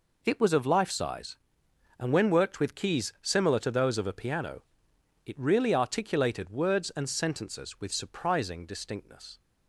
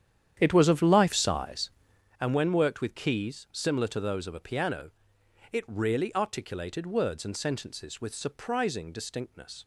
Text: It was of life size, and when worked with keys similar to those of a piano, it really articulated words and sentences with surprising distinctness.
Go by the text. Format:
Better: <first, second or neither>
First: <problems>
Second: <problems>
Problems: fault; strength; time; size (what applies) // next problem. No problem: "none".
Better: first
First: none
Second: starts louder than the rest; strong; until 2.2 s; 9.5 dB